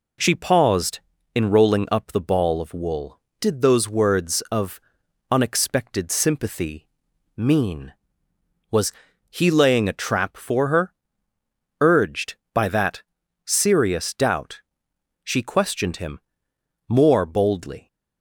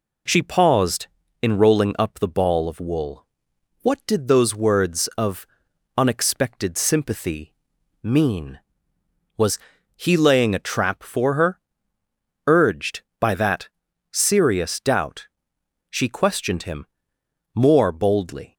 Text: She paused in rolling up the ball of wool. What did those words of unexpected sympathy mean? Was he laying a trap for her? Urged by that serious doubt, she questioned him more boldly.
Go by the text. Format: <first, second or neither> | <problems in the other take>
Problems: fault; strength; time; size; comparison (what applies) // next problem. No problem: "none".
second | skips "What"; at 3.3 s // pauses between "of" and "unexpected"; noticeable; at 4.7 s; 0.50 s long; noticeable in the second // pauses between "sympathy" and "mean"; noticeable; at 6.8 s; 0.48 s long; noticeable in the second // pauses between "Was" and "he"; slight; at 8.9 s; 0.36 s long; slight in the second // pauses between "that" and "serious"; at 13.0 s; 0.42 s long; also in the second // pauses between "him" and "more"; noticeable; at 16.2 s; 0.66 s long; noticeable in the second